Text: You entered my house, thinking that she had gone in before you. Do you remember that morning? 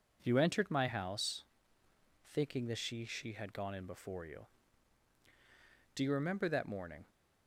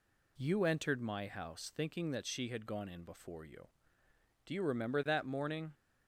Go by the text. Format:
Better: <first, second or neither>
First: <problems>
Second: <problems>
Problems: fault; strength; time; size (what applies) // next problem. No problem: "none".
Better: second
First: says "she" twice; at 3.0 s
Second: none